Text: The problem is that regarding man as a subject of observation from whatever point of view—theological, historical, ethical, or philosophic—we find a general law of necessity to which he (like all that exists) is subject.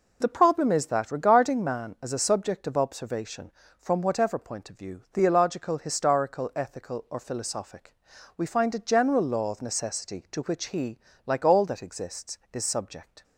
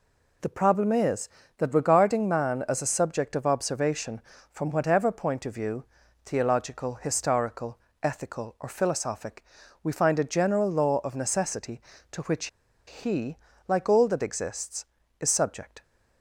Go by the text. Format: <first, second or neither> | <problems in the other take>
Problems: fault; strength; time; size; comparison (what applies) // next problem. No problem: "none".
first | pauses between "which" and "he"; at 12.4 s; 0.40 s long